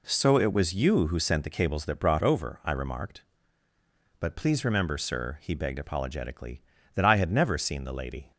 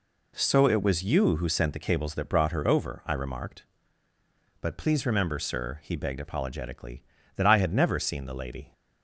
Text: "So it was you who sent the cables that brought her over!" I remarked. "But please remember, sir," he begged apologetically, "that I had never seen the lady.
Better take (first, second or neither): second